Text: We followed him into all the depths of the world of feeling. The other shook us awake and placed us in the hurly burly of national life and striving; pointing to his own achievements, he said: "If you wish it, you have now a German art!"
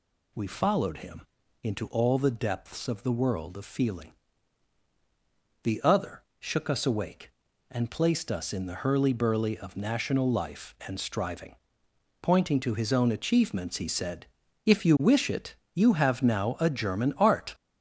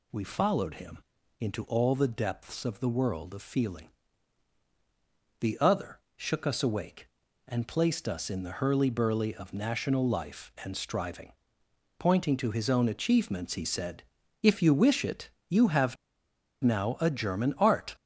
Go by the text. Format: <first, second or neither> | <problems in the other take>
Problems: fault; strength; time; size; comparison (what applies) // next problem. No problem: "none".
first | pauses between "him" and "into"; at 0.9 s; 0.42 s long; also in the first // pauses between "other" and "shook"; slight; at 6.0 s; 0.16 s long; slight in the first // pauses between "have" and "now"; noticeable; at 15.9 s; 0.68 s long